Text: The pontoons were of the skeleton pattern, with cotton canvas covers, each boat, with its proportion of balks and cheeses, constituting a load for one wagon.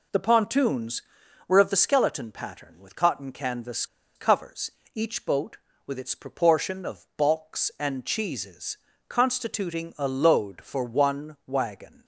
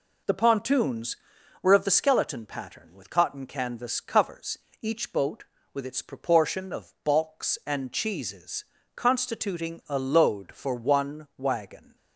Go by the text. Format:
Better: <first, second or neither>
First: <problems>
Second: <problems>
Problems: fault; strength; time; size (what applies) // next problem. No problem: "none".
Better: second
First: pauses between "canvas" and "covers"; slight; at 3.8 s; 0.30 s long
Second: none